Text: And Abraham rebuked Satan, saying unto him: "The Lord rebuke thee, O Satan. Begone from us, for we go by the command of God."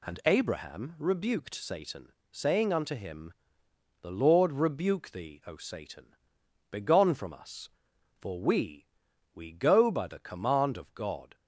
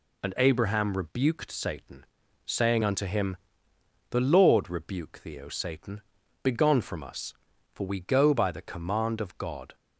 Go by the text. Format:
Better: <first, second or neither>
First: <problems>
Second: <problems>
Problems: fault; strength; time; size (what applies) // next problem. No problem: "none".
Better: second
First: says "we" twice; at 9.3 s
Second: none